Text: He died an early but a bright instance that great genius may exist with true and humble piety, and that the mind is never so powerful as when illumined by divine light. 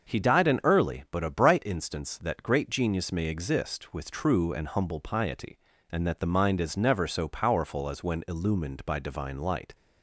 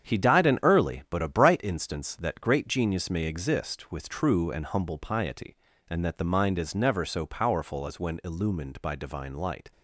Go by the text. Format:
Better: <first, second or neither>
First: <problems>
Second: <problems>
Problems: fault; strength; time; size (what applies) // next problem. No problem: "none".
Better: first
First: starts louder than the rest; until 1.2 s; 6.5 dB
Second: gets quieter; strong; throughout; 8 dB // starts louder than the rest; strong; until 1.1 s; 8.5 dB